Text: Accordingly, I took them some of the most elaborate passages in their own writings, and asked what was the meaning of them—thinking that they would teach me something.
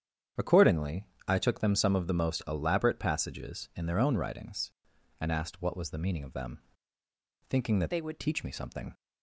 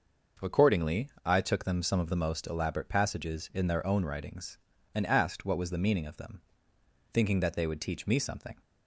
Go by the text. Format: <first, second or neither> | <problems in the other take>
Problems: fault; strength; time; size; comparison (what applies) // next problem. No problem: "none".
second | starts louder than the rest; strong; until 1.5 s; 8.5 dB; noticeable in the second // changes voice from "they" to "would"; from 7.9 to 8.2 s; 0.3 s long